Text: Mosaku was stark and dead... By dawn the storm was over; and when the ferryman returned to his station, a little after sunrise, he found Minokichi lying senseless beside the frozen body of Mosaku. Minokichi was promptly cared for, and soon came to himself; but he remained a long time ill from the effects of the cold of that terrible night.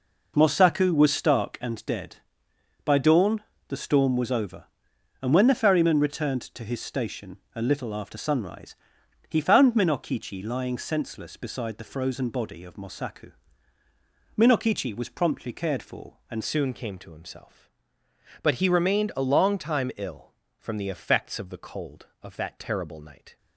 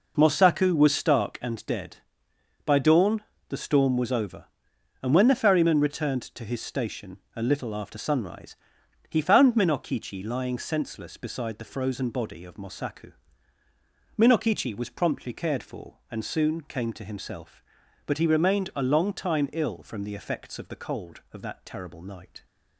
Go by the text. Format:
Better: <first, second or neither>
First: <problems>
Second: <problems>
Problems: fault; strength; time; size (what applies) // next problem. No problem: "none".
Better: second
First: pauses between "dawn" and "the"; slight; at 3.4 s; 0.28 s long // changes voice at "soon"; from 16.4 s on; 6.9 s long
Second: pauses between "dawn" and "the"; slight; at 3.2 s; 0.28 s long